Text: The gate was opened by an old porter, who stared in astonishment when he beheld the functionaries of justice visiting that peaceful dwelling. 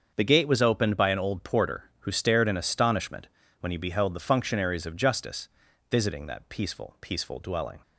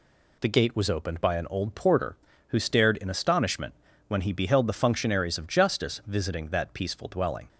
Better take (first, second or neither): second